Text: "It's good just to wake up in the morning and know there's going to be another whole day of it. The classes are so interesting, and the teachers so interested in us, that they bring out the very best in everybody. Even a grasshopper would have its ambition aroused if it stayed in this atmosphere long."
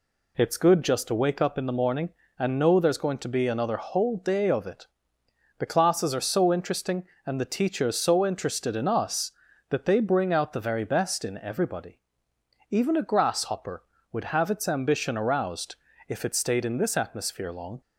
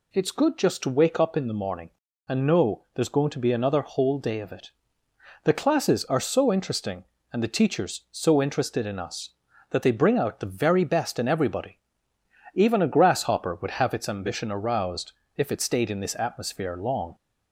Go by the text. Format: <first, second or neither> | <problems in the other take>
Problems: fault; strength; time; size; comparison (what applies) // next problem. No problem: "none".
neither | pauses between "aroused" and "if"; slight; the same in both